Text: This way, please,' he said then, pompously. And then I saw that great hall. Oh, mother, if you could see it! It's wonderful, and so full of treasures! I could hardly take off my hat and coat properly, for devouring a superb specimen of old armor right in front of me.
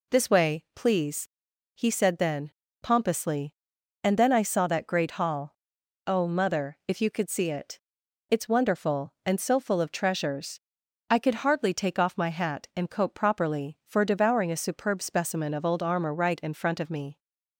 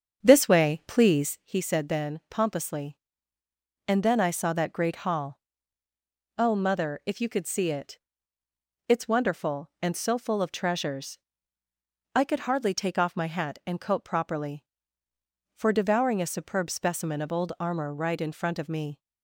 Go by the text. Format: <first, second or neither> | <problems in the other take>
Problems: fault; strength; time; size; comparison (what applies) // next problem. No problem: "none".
first | starts louder than the rest; strong; until 1.5 s; 7 dB